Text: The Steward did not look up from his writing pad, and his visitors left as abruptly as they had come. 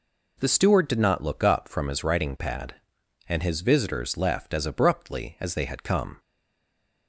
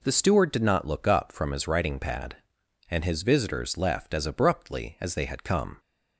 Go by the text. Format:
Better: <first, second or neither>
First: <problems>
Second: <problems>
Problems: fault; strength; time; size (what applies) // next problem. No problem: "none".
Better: second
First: stays silent after the last word; slight; from 6.1 s on; 0.9 s long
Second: none